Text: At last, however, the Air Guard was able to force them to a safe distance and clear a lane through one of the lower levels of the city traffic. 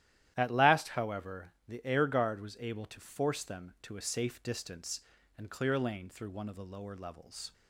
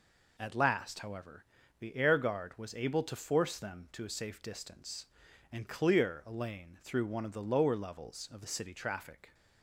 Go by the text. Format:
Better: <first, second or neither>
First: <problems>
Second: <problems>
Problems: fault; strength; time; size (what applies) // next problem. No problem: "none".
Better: second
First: starts louder than the rest; strong; until 1.3 s; 12.5 dB // stops before "of the city traffic"; at 7.5 s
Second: none